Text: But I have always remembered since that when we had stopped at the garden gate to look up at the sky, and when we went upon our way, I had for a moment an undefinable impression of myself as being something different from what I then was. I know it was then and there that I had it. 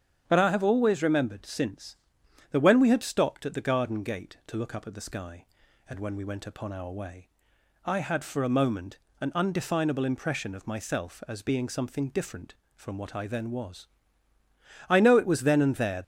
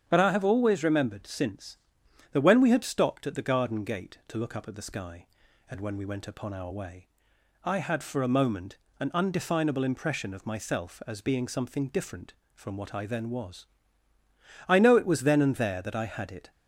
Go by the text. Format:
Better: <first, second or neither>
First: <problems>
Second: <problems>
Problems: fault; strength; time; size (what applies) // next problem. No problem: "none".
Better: second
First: starts louder than the rest; strong; until 1.2 s; 8.5 dB // pauses between "moment" and "an"; slight; at 8.9 s; 0.22 s long // stops before "that I had it"; at 16.0 s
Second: starts louder than the rest; strong; until 1.0 s; 8.5 dB // pauses between "moment" and "an"; slight; at 8.7 s; 0.22 s long